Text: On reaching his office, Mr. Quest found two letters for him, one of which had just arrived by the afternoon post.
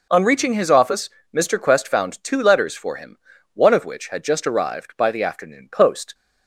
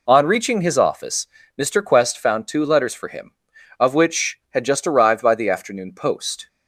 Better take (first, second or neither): first